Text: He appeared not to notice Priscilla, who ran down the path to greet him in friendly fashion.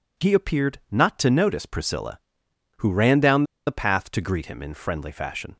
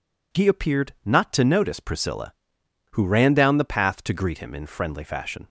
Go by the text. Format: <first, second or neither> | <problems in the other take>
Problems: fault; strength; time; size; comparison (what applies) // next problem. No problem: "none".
second | pauses between "down" and "the"; slight; at 3.4 s; 0.23 s long